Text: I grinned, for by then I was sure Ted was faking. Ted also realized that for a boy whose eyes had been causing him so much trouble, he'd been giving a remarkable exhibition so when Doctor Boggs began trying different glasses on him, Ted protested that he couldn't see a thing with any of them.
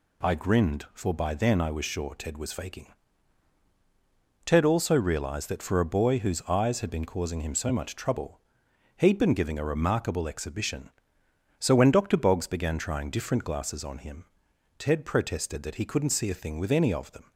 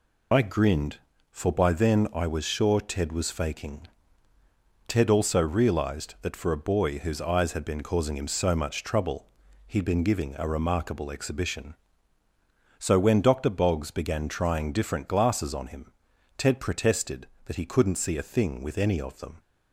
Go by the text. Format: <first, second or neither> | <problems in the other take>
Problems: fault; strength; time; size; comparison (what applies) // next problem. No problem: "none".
first | loses the start of "I"; at 0.3 s; 35 ms